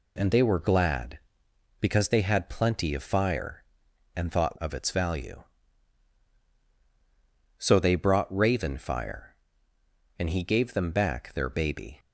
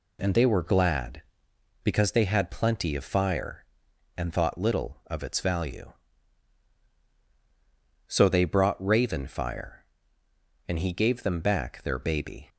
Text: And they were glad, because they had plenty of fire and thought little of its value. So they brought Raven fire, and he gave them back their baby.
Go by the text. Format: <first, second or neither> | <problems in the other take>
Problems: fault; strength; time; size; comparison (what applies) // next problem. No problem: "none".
second | skips "little"; at 4.5 s